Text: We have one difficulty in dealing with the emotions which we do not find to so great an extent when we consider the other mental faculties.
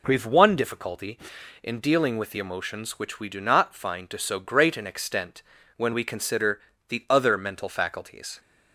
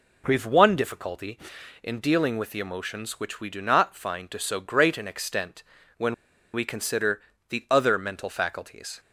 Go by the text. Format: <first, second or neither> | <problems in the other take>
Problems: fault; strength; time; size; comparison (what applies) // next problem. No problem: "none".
first | pauses between "extent" and "when"; slight; at 5.6 s; 0.34 s long; slight in the first // pauses between "when" and "we"; at 6.1 s; 0.39 s long // pauses between "consider" and "the"; slight; at 7.1 s; 0.30 s long; slight in the first